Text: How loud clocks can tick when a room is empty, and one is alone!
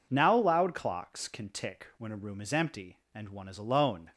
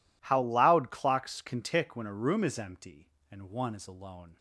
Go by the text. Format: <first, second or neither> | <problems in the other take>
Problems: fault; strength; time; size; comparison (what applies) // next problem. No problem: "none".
second | says "Now" for "How"; at 0.1 s